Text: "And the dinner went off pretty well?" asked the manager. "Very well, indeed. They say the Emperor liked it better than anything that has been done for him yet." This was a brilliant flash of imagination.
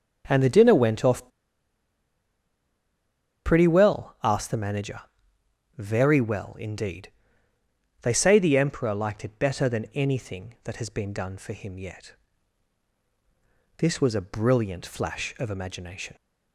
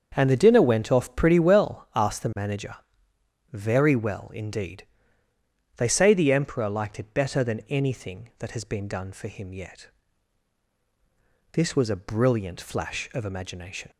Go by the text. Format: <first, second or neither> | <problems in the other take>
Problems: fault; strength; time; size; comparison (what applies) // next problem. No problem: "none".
second | starts louder than the rest; until 1.2 s; 7 dB; also in the second // pauses between "off" and "pretty"; strong; at 1.2 s; 2.1 s long